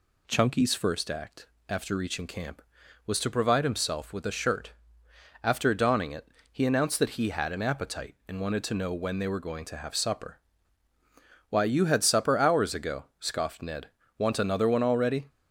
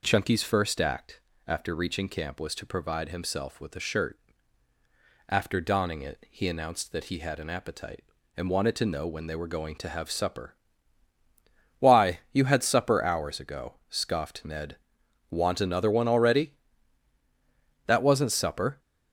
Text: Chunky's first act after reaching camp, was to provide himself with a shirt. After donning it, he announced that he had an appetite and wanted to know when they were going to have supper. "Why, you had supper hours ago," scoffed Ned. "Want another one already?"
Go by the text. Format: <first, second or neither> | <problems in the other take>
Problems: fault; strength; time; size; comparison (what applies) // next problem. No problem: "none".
first | pauses between "act" and "after"; slight; at 1.2 s; 0.28 s long; slight in the first // goes on to say "That wasn't supper"; noticeable; from 17.8 s on; 0.92 s long